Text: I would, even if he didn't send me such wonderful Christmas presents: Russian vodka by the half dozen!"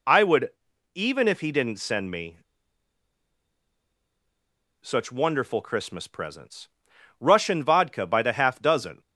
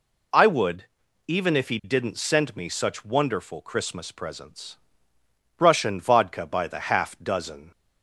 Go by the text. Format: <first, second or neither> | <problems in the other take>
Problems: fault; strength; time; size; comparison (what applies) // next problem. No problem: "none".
second | pauses between "me" and "such"; strong; at 2.3 s; 2.4 s long